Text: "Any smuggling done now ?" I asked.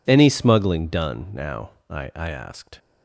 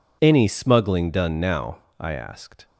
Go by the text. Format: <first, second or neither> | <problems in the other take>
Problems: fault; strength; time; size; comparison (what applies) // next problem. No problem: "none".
second | says "I" twice; at 2.1 s